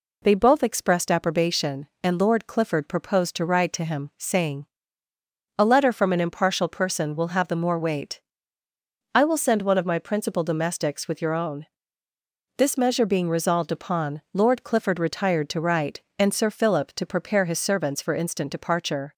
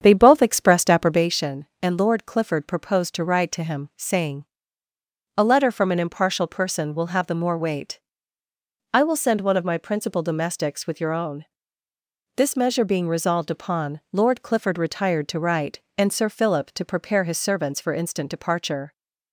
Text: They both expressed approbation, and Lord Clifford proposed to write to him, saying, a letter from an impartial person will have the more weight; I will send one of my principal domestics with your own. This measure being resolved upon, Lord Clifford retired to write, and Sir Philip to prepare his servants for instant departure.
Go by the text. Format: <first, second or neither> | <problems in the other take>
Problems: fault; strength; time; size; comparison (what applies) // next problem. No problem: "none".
first | starts louder than the rest; strong; until 1.3 s; 8 dB